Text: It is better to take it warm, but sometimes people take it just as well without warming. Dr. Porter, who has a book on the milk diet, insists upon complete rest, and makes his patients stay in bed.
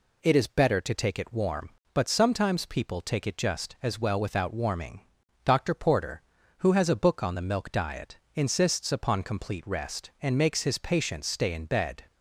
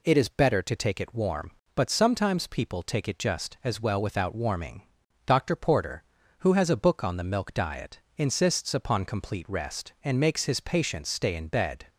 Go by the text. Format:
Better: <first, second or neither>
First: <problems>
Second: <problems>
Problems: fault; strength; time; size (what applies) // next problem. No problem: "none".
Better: neither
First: none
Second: none